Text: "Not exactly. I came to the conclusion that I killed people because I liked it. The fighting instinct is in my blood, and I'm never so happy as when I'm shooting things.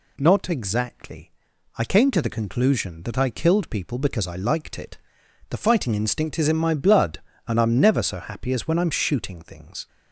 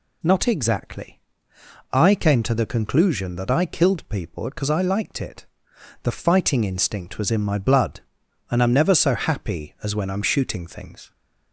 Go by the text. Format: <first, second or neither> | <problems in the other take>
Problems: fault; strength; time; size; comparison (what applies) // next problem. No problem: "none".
first | says "was" for "is"; at 7.1 s